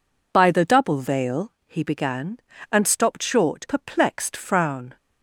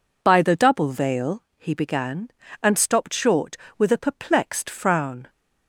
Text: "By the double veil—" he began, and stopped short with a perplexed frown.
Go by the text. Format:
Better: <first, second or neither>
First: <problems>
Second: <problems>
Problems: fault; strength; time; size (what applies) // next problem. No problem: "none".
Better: second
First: skips "with a"; at 3.6 s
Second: none